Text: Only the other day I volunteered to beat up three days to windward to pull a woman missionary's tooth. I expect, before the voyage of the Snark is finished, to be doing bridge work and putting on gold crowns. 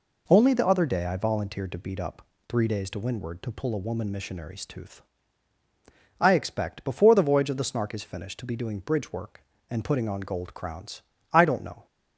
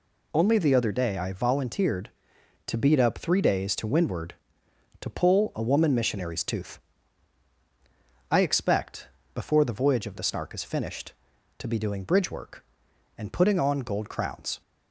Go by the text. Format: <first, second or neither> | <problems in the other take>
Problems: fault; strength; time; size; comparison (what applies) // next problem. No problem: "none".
second | pauses between "up" and "three"; slight; at 2.2 s; 0.22 s long // goes on to say "I don't know"; from 11.3 s on; 0.54 s long